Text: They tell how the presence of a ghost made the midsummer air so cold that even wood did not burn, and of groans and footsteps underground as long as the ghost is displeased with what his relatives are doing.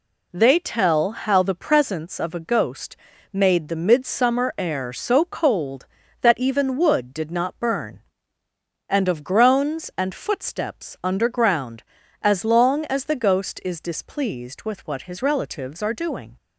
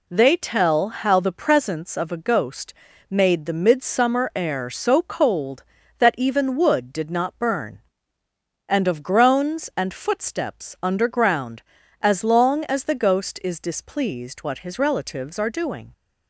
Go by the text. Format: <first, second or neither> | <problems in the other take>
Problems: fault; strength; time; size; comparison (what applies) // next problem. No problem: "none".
first | pauses between "ghost" and "made"; slight; at 2.7 s; 0.36 s long; slight in the first // skips "with"; at 14.4 s